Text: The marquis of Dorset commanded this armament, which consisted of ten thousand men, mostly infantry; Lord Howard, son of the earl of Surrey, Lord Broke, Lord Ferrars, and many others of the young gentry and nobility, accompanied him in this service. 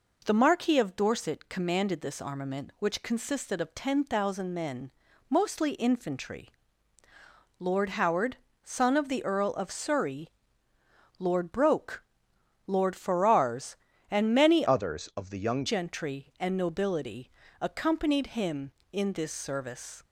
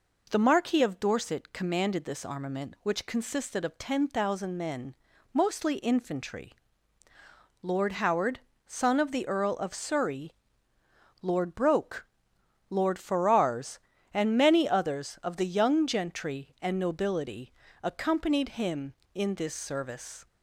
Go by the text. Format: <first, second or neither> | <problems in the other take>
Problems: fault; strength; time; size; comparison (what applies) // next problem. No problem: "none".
second | changes voice from "others" to "young"; from 14.6 to 15.6 s; 1.0 s long